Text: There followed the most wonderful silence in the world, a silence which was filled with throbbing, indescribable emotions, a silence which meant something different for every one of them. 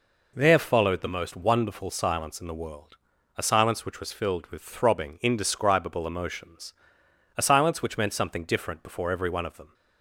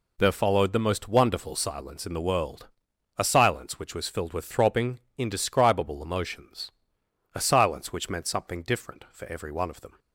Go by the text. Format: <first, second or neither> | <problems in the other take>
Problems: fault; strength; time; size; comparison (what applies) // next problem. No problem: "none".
second | says "before" for "for"; at 8.8 s